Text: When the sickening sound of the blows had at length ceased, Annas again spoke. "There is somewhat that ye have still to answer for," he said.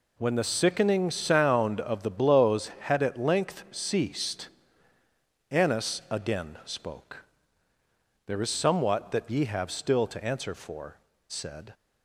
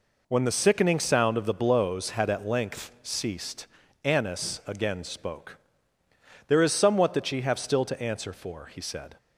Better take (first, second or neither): second